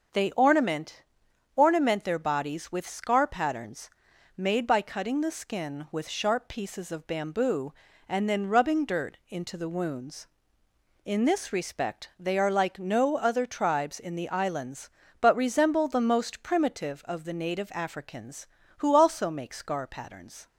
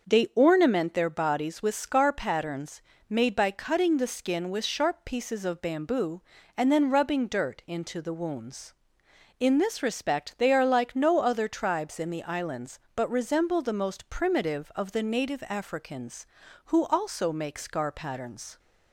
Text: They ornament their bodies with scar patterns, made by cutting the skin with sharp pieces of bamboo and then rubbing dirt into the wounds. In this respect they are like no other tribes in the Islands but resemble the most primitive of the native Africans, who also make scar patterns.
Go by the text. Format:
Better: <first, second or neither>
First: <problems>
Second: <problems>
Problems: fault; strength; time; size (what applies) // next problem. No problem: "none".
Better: second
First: starts louder than the rest; until 1.6 s; 6 dB // says "ornament" twice; at 1.5 s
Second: starts louder than the rest; noticeable; until 1.1 s; 6 dB